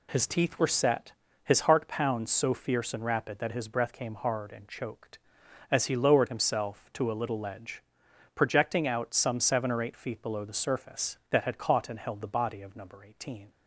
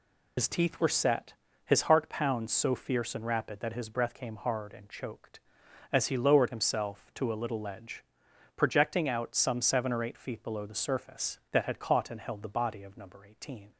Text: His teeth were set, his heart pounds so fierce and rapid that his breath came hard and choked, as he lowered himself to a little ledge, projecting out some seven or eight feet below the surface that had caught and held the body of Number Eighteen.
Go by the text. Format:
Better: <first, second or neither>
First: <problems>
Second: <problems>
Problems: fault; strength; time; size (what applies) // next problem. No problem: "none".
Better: first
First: none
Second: loses the start of "His"; at 0.3 s; 75 ms